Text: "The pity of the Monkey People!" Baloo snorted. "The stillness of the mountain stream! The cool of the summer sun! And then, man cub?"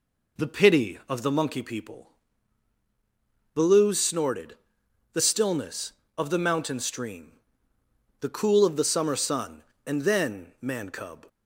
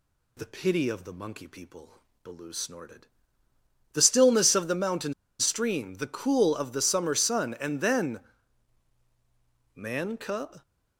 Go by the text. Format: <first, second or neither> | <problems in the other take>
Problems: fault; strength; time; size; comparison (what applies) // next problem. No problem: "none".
first | pauses between "mountain" and "stream"; slight; at 5.1 s; 0.27 s long